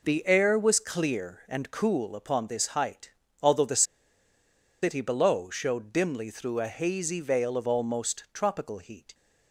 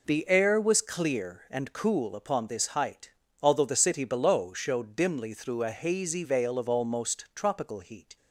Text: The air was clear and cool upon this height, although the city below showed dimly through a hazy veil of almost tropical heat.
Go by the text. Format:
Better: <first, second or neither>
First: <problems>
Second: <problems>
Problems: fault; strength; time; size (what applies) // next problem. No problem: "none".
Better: second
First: pauses between "the" and "city"; at 3.8 s; 0.99 s long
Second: none